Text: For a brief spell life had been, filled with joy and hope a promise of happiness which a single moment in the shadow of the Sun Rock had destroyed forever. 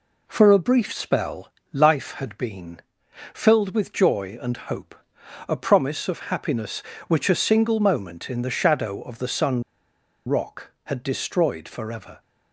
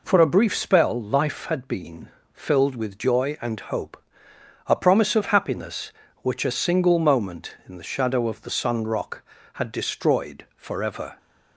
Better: second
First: pauses between "spell" and "life"; slight; at 1.5 s; 0.22 s long // pauses between "hope" and "a"; noticeable; at 4.9 s; 0.56 s long // pauses between "Sun" and "Rock"; noticeable; at 9.6 s; 0.65 s long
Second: pauses between "hope" and "a"; noticeable; at 4.0 s; 0.64 s long

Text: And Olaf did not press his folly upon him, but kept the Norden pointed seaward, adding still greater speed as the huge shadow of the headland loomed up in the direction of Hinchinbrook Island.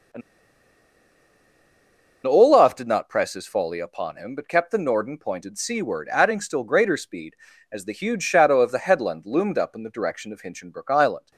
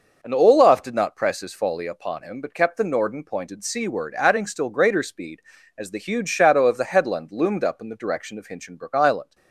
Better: second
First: pauses between "And" and "Olaf"; strong; at 0.2 s; 2.0 s long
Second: none

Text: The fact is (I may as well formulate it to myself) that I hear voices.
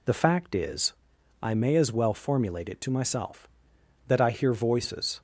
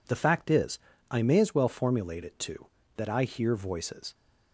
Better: first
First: none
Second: skips "myself"; at 2.8 s

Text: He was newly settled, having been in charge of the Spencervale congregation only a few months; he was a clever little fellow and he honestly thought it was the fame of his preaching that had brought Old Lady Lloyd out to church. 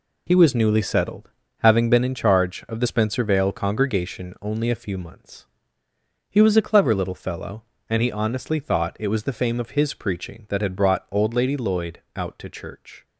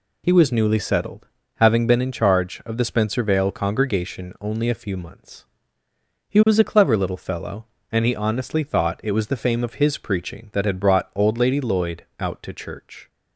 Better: second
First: gets quieter; strong; throughout; 8.5 dB // pauses between "Lloyd" and "out"; slight; at 12.0 s; 0.16 s long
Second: pauses between "Lloyd" and "out"; slight; at 12.0 s; 0.16 s long

